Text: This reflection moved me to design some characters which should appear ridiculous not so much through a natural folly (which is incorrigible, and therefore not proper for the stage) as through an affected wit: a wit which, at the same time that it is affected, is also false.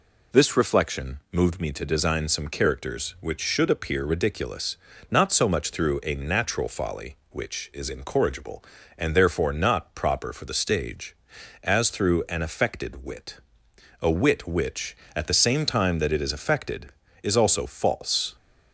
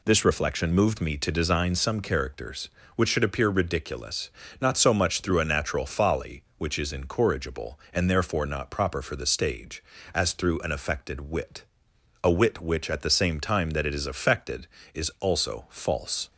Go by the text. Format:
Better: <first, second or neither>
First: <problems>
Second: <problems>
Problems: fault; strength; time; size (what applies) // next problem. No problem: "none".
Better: neither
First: pauses between "ridiculous" and "not"; slight; at 4.7 s; 0.32 s long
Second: pauses between "ridiculous" and "not"; slight; at 4.3 s; 0.30 s long